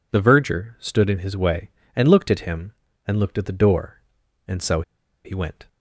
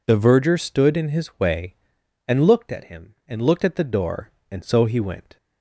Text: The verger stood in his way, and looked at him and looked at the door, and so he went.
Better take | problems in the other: second | pauses between "so" and "he"; at 4.8 s; 0.43 s long

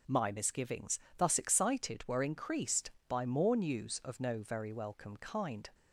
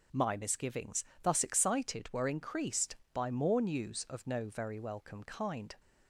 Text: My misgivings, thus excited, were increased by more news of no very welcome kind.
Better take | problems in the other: neither | none

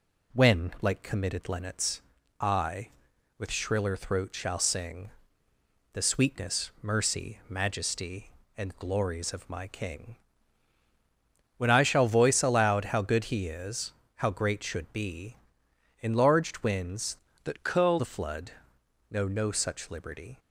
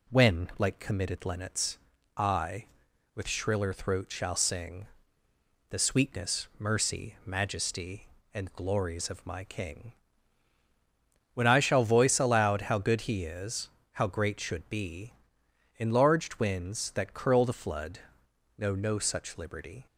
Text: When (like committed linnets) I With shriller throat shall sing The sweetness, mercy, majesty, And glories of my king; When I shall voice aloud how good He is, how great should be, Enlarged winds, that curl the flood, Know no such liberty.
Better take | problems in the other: second | pauses between "sing" and "The"; noticeable; at 5.1 s; 0.82 s long; noticeable in the second // changes voice from "that" to "curl"; from 17.4 to 17.9 s; 0.5 s long

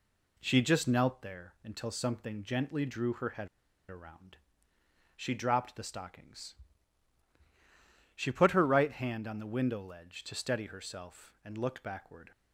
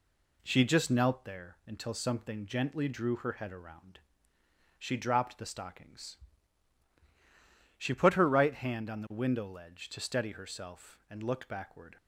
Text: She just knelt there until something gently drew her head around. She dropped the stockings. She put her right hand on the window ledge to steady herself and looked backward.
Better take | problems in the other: second | pauses between "head" and "around"; at 3.4 s; 0.40 s long

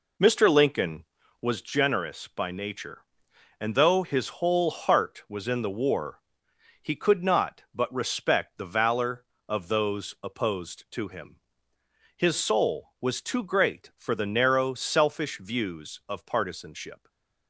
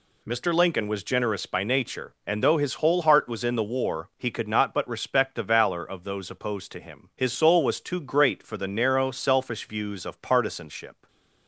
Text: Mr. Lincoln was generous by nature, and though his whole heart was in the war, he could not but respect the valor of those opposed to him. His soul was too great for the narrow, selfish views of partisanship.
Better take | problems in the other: second | starts louder than the rest; until 1.6 s; 3.5 dB // stays silent after the last word; slight; from 16.9 s on; 0.5 s long

